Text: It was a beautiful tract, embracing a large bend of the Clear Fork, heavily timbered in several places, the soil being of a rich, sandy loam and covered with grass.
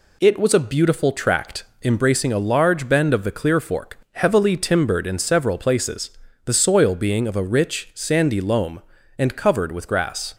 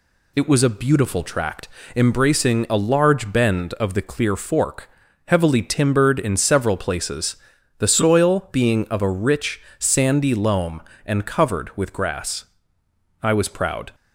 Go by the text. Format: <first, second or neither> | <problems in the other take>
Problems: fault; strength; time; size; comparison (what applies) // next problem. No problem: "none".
first | goes on to say "I was proud"; noticeable; from 13.2 s on; 0.72 s long